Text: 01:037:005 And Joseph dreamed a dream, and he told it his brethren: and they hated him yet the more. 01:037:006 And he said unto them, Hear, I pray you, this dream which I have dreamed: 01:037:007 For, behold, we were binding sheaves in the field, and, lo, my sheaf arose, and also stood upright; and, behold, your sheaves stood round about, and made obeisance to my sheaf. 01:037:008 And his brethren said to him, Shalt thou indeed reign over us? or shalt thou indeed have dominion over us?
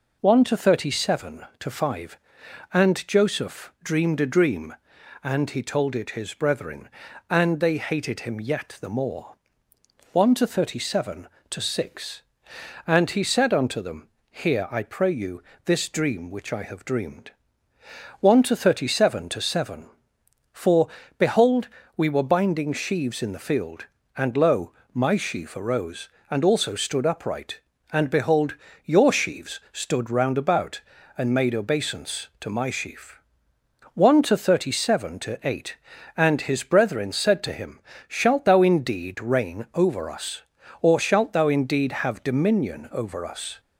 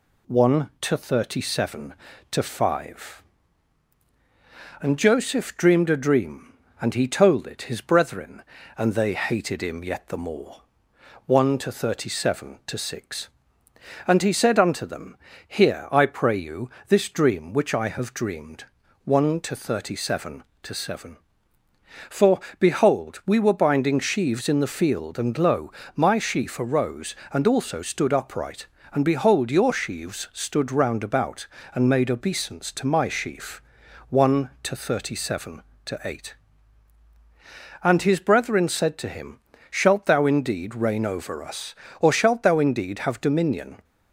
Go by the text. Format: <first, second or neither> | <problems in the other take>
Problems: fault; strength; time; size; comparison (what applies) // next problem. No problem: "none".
first | stops before "over us"; at 43.8 s